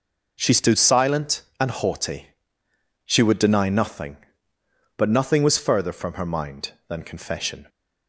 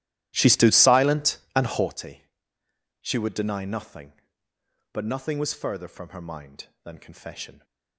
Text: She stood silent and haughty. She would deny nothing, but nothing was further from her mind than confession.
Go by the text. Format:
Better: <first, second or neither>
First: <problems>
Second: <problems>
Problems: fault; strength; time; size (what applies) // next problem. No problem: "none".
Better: first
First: none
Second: starts louder than the rest; strong; until 1.9 s; 14 dB